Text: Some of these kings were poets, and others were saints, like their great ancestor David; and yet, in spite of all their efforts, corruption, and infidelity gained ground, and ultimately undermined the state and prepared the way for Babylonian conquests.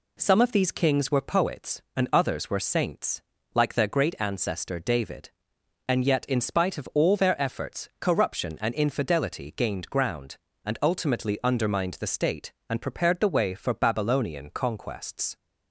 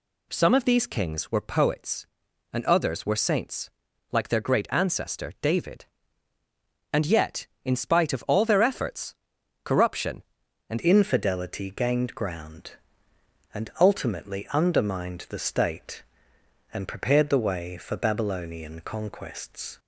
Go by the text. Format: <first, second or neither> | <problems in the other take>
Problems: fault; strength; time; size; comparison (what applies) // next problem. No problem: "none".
first | changes voice at "infidelity"; from 10.8 s on; 8.9 s long